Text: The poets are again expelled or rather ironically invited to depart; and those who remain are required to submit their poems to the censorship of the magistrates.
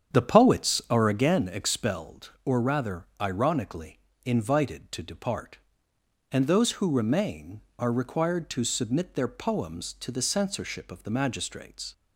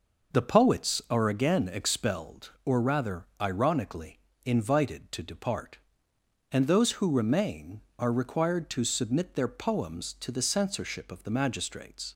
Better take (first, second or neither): second